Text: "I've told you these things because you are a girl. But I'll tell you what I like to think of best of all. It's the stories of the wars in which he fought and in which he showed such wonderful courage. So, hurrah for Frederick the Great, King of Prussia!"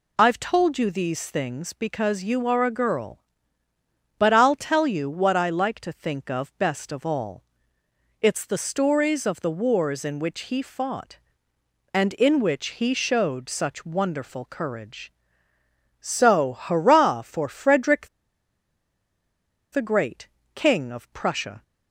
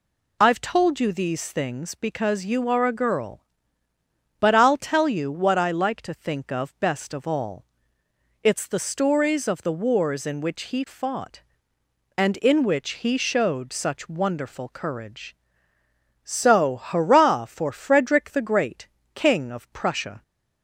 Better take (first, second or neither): second